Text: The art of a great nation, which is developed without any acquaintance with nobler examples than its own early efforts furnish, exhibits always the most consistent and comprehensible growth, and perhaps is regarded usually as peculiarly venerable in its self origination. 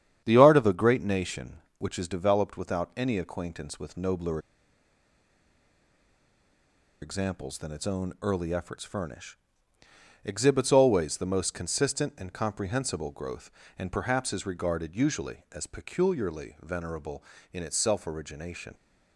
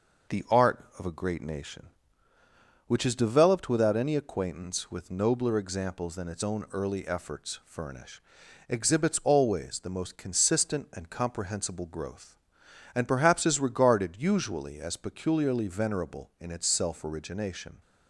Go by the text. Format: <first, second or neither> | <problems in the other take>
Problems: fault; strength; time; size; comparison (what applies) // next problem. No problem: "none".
second | starts louder than the rest; strong; until 1.2 s; 9 dB // pauses between "nobler" and "examples"; strong; at 4.3 s; 2.6 s long